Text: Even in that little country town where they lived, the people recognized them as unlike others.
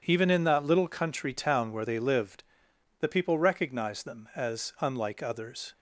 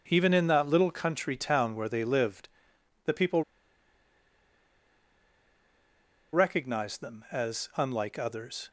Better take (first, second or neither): first